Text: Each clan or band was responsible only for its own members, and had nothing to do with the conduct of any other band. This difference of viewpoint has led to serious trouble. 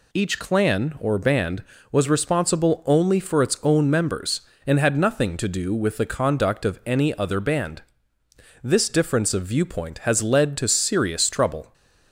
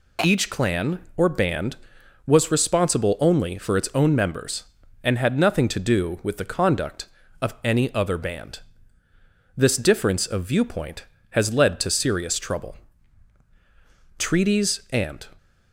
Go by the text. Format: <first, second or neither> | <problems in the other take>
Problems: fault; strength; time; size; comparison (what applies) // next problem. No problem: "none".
first | goes on to say "TREATIES AND"; noticeable; from 14.1 s on; 1.1 s long